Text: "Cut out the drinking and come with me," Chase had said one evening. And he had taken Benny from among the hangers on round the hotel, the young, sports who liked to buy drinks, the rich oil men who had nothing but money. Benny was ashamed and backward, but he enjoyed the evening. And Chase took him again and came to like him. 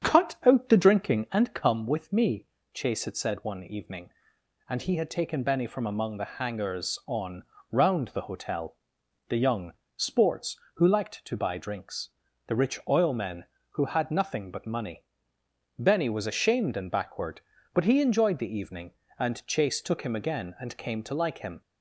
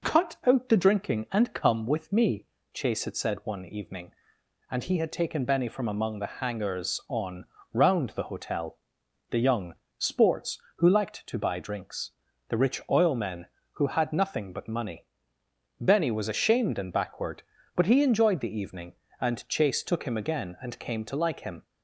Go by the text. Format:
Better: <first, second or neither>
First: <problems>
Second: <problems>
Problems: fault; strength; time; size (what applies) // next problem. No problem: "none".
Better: second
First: starts louder than the rest; strong; until 1.4 s; 8.5 dB // pauses between "on" and "round"; slight; at 7.4 s; 0.28 s long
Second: pauses between "on" and "round"; slight; at 7.4 s; 0.28 s long